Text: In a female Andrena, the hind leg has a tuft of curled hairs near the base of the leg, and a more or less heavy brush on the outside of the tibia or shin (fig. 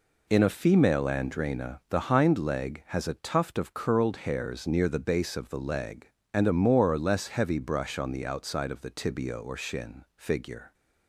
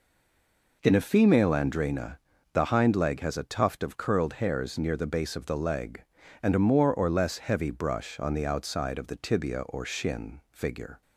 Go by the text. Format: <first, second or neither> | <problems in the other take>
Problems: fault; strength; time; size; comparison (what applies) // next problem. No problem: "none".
first | stays silent before the first word; slight; until 0.8 s; 0.8 s long